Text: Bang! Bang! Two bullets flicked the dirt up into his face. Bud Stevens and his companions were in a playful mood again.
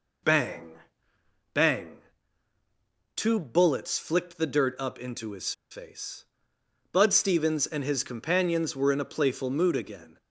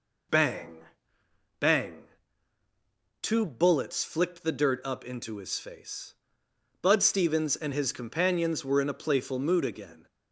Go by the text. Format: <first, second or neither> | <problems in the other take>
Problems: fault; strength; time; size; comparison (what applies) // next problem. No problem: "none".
second | pauses between "his" and "face"; slight; at 5.5 s; 0.18 s long